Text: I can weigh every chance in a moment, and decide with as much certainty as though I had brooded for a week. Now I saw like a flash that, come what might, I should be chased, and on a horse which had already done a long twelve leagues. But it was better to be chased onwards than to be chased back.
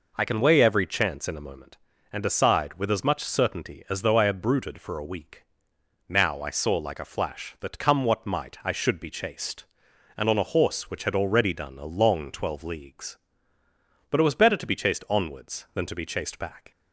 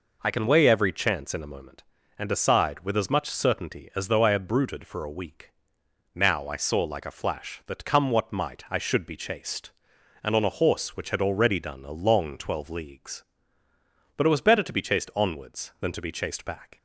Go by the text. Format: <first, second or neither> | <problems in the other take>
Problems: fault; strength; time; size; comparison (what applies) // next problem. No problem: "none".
neither | none